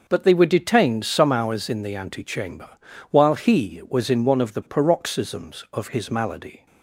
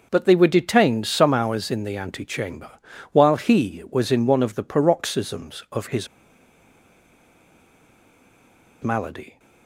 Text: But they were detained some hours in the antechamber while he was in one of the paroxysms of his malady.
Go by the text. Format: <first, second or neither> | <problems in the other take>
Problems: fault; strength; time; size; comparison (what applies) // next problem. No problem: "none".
first | pauses between "antechamber" and "while"; at 2.7 s; 0.42 s long; also in the first // pauses between "his" and "malady"; strong; at 6.0 s; 2.7 s long